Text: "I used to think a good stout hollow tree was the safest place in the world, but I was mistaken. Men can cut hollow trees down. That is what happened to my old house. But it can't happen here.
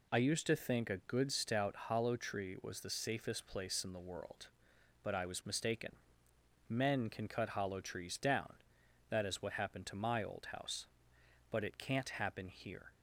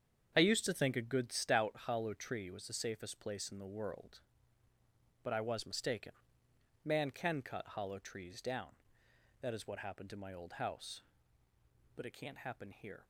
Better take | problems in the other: first | starts louder than the rest; strong; until 1.3 s; 7.5 dB // says "Man" for "Men"; at 6.8 s

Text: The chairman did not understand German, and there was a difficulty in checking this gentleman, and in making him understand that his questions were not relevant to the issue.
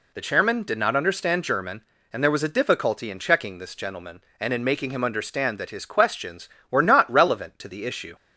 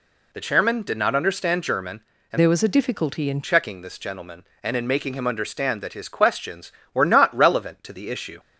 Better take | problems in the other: first | changes voice from "there" to "in"; from 2.3 to 3.4 s; 1.1 s long

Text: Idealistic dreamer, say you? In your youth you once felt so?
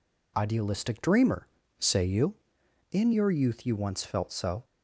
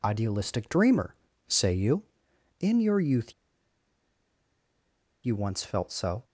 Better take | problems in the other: first | pauses between "youth" and "you"; strong; at 3.3 s; 1.9 s long

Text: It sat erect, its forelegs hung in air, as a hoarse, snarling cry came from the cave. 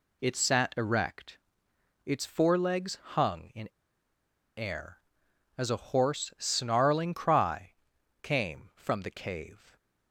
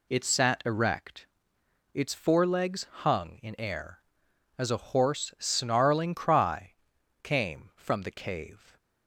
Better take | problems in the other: second | pauses between "in" and "air"; noticeable; at 3.6 s; 0.89 s long // pauses between "cry" and "came"; noticeable; at 7.7 s; 0.50 s long; noticeable in the second

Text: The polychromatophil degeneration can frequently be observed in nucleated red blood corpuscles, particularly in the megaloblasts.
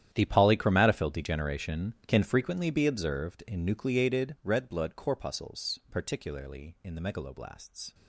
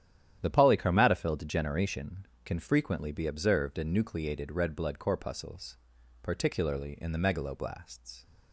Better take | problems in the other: second | gets quieter; strong; throughout; 16.5 dB // starts louder than the rest; strong; until 1.1 s; 10.5 dB; strong in the second

